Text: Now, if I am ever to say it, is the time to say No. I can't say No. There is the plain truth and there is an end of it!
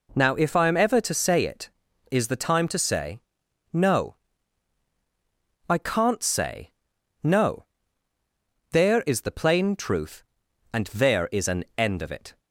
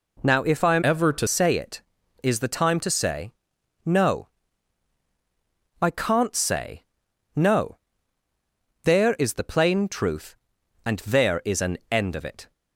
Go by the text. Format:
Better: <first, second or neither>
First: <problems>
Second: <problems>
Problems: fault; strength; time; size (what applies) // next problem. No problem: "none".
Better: first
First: pauses between "say" and "No"; noticeable; at 3.2 s; 0.51 s long // pauses between "say" and "No"; noticeable; at 6.7 s; 0.50 s long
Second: changes voice from "ever" to "to"; from 0.8 to 1.2 s; 0.4 s long // pauses between "say" and "No"; noticeable; at 3.3 s; 0.52 s long // pauses between "say" and "No"; noticeable; at 6.8 s; 0.50 s long